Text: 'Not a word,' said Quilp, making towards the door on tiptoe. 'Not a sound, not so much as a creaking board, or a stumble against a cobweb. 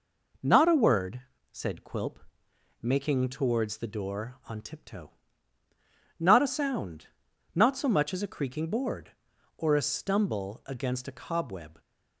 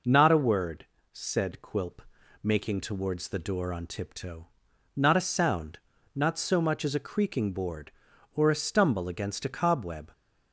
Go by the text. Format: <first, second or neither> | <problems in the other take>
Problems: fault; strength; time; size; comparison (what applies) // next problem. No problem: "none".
neither | none